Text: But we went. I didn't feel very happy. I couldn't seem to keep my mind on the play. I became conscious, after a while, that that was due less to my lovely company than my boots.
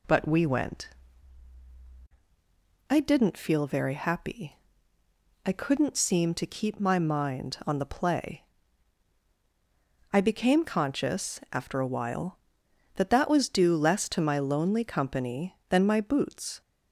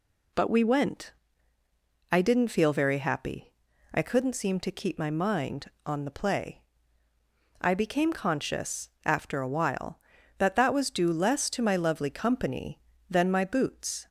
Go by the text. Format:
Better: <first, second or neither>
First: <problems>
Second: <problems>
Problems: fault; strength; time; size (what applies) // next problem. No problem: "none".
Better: second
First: says "lonely" for "lovely"; at 14.3 s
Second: none